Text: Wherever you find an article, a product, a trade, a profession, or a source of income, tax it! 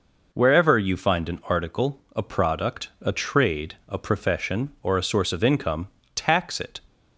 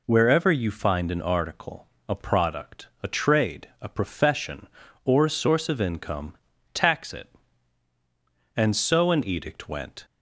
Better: first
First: none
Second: goes on to say "And so an edict went"; from 8.5 s on; 1.5 s long

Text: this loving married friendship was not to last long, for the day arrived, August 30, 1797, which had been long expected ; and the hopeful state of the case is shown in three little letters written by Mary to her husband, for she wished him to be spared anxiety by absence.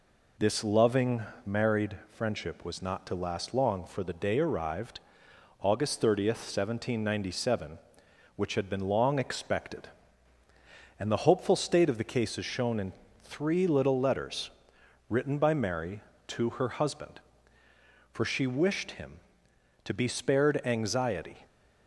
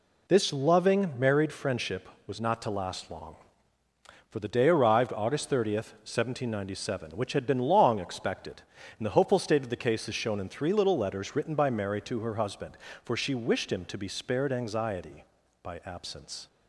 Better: second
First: pauses between "loving" and "married"; slight; at 1.2 s; 0.22 s long // pauses between "in" and "three"; slight; at 12.9 s; 0.30 s long // pauses between "letters" and "written"; noticeable; at 14.4 s; 0.60 s long // stops before "by absence"; at 21.4 s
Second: none

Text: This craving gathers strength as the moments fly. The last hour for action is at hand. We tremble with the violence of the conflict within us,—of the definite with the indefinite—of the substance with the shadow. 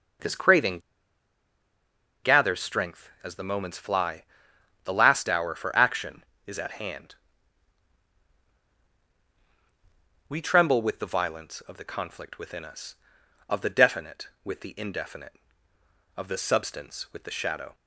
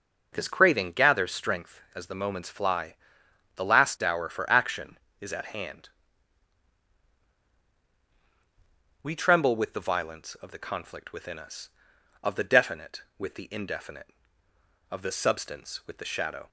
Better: second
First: pauses between "craving" and "gathers"; strong; at 0.7 s; 1.4 s long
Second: none

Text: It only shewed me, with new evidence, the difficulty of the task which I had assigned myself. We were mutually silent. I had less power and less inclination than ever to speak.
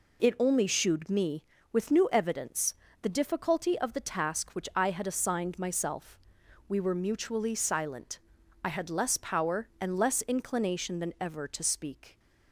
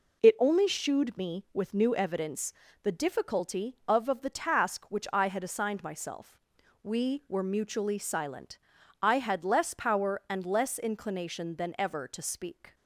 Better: first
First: none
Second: says "of" twice; at 4.0 s

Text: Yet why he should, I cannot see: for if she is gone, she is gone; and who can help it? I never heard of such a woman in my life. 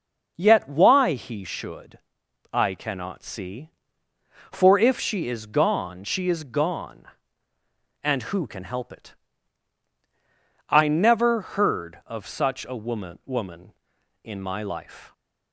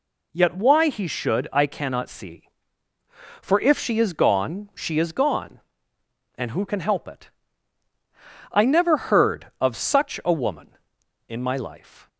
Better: second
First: says "woman" twice; at 13.2 s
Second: none

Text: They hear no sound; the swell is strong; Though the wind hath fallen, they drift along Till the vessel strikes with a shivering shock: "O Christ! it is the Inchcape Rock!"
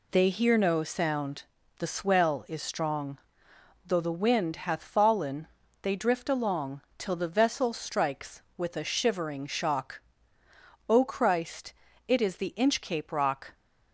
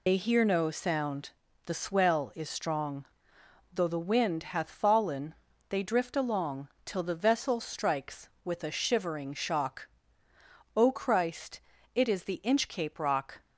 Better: first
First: pauses between "along" and "Till"; slight; at 6.8 s; 0.16 s long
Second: loses the start of "They"; at 0.0 s; 80 ms // pauses between "along" and "Till"; slight; at 6.6 s; 0.16 s long

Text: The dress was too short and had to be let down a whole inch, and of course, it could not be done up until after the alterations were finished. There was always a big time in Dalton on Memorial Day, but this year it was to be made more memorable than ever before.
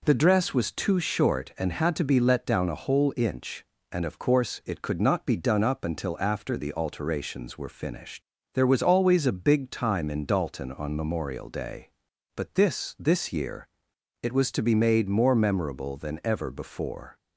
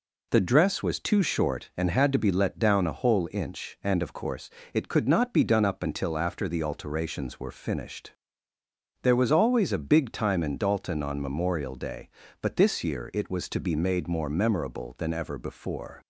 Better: second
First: says "this" twice; at 12.9 s // pauses between "year" and "it"; noticeable; at 13.6 s; 0.56 s long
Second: none

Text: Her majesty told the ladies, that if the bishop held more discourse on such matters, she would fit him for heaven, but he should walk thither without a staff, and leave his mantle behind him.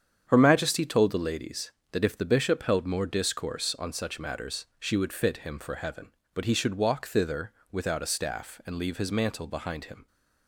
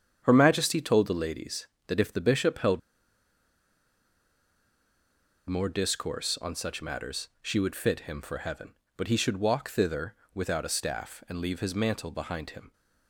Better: first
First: starts louder than the rest; strong; until 1.2 s; 8 dB // pauses between "thither" and "without"; slight; at 7.5 s; 0.20 s long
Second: starts louder than the rest; strong; until 1.2 s; 8.5 dB // pauses between "held" and "more"; strong; at 2.7 s; 2.6 s long // pauses between "thither" and "without"; slight; at 10.1 s; 0.20 s long

